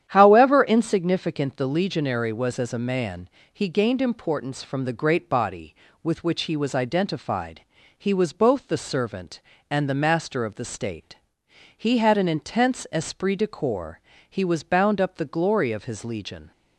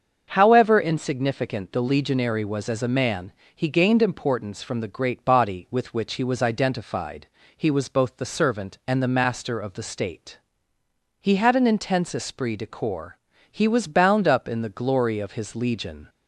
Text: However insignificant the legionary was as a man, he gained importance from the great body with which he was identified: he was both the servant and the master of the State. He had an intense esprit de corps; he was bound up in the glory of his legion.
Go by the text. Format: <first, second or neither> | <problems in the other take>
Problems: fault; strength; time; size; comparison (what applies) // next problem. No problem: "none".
second | starts louder than the rest; strong; until 1.0 s; 10 dB; also in the second // skips "in"; at 15.1 s